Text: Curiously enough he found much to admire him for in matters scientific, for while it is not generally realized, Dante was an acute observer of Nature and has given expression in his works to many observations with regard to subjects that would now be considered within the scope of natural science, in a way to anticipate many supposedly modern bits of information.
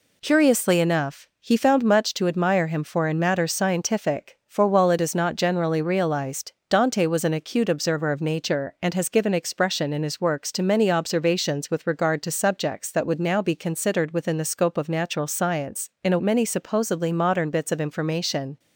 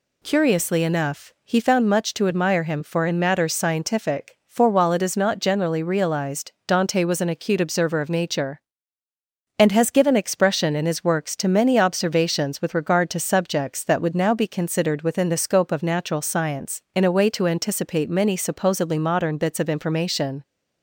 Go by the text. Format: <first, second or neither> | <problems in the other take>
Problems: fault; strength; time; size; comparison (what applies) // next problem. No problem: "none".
second | skips "way to anticipate"; at 16.2 s